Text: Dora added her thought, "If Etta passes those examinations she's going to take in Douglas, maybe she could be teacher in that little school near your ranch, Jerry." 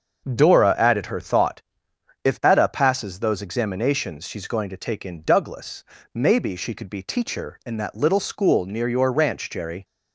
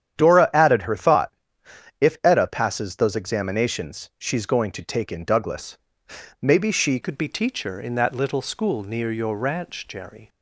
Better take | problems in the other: first | starts louder than the rest; strong; until 1.2 s; 9.5 dB; also in the first // changes voice at "could"; from 7.0 s on; 3.2 s long

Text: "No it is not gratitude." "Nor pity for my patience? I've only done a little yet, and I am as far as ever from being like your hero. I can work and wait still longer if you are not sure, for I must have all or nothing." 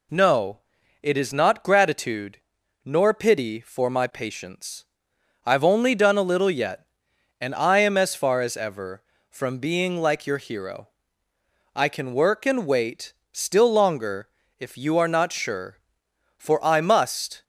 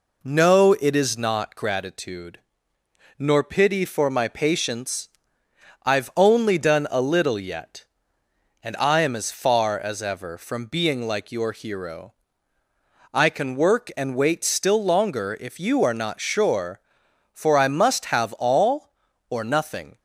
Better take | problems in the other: second | pauses between "No" and "it"; noticeable; at 0.5 s; 0.46 s long // pauses between "wait" and "still"; slight; at 13.1 s; 0.18 s long // pauses between "longer" and "if"; slight; at 14.2 s; 0.32 s long // stops before "have all or nothing"; at 17.4 s

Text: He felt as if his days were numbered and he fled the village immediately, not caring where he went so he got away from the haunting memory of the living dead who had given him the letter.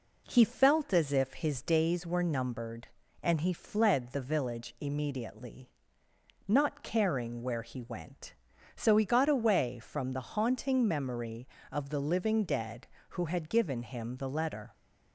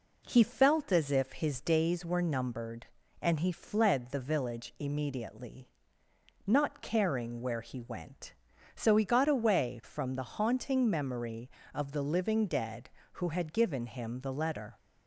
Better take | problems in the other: neither | none

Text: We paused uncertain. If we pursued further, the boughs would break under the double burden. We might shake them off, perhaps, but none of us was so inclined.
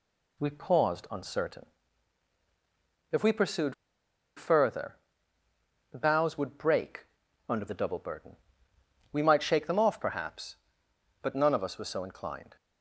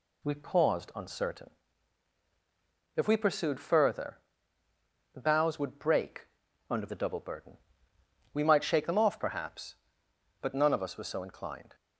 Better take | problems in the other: second | pauses between "pursued" and "further"; noticeable; at 3.7 s; 0.63 s long // pauses between "break" and "under"; at 7.0 s; 0.42 s long; also in the second

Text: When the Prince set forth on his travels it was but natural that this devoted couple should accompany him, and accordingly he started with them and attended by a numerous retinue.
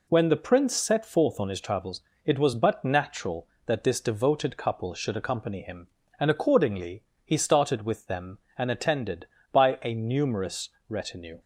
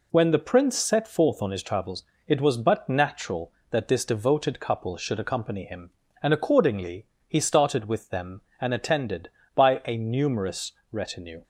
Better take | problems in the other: neither | pauses between "travels" and "it"; slight; the same in both // pauses between "accordingly" and "he"; slight; the same in both // pauses between "numerous" and "retinue"; slight; the same in both

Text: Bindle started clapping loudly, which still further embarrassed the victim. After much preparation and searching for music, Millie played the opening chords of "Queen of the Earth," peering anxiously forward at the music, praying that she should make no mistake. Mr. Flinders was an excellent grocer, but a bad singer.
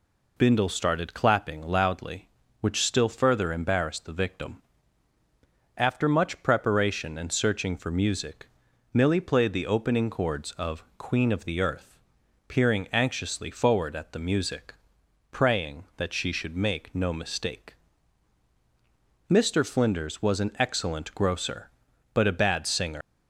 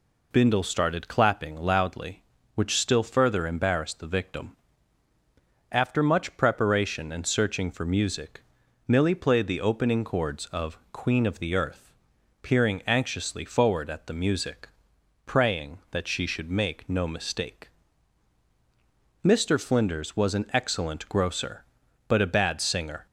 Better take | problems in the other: second | leaves "singer" unfinished; at 23.0 s; 105 ms

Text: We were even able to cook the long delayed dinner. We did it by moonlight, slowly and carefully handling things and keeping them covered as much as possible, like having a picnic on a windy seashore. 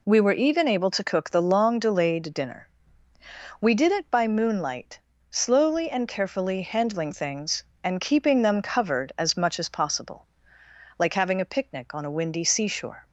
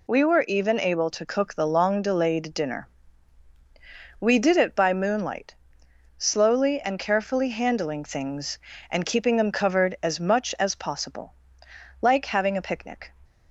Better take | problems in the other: first | stops before "on a windy seashore"; at 13.2 s

